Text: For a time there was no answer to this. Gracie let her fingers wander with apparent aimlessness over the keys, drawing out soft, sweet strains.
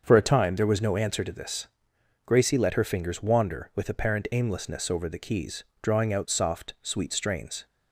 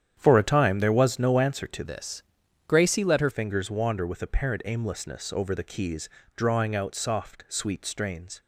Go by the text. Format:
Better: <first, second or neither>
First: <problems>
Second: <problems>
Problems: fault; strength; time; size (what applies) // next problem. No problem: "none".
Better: first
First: starts louder than the rest; until 1.0 s; 7 dB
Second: starts louder than the rest; strong; until 1.1 s; 9.5 dB // changes voice from "this" to "her"; from 1.8 to 3.3 s; 1.5 s long